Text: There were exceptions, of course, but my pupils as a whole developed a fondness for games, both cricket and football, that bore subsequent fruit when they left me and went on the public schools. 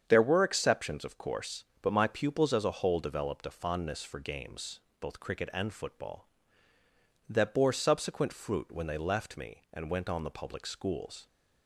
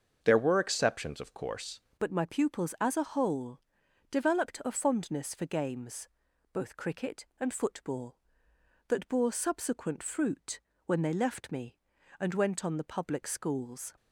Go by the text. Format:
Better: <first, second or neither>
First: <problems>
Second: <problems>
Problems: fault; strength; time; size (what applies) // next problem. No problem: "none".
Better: first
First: starts louder than the rest; strong; until 1.0 s; 7.5 dB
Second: starts louder than the rest; until 1.2 s; 6.5 dB // changes voice at "but"; from 1.9 s on; 12.0 s long // pauses between "whole" and "developed"; noticeable; at 3.5 s; 0.50 s long // pauses between "fruit" and "when"; slight; at 10.5 s; 0.26 s long